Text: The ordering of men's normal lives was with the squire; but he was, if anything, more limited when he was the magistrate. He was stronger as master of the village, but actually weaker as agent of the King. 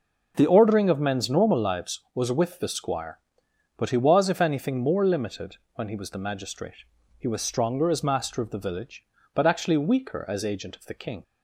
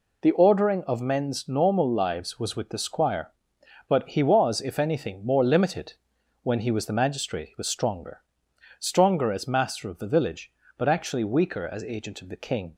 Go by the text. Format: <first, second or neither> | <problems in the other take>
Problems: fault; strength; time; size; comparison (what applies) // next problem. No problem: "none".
first | pauses between "limited" and "when"; noticeable; at 5.9 s; 0.48 s long; slight in the first // says "stronger" twice; at 8.7 s